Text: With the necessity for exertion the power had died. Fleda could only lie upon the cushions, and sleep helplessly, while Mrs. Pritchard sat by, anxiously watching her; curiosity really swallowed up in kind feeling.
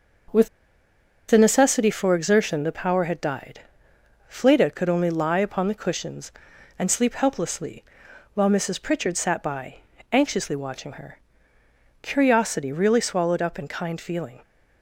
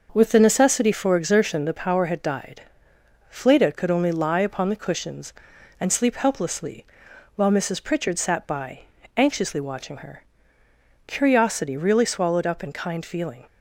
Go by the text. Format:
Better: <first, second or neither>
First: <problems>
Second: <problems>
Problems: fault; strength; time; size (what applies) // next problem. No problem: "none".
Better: second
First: starts louder than the rest; until 2.1 s; 6 dB // pauses between "With" and "the"; noticeable; at 0.4 s; 0.82 s long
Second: starts louder than the rest; noticeable; until 1.1 s; 6 dB